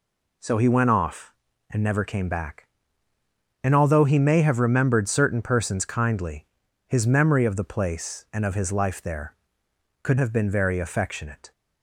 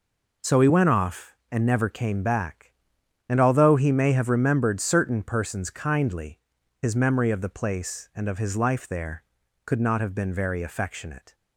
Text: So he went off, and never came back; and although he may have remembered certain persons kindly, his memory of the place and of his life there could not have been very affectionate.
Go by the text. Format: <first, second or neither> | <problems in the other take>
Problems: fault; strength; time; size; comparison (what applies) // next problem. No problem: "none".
second | skips "not"; at 10.1 s